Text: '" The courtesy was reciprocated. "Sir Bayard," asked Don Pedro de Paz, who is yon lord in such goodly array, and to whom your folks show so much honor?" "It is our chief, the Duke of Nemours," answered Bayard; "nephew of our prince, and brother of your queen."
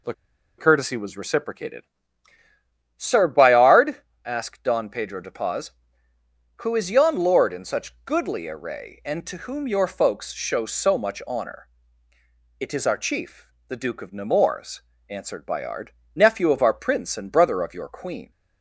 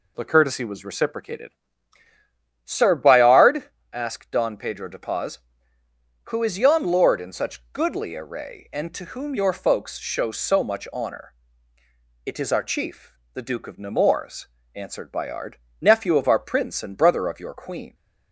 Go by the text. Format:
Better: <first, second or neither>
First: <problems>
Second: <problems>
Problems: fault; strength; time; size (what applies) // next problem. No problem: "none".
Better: second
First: pauses between "The" and "courtesy"; at 0.1 s; 0.45 s long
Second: none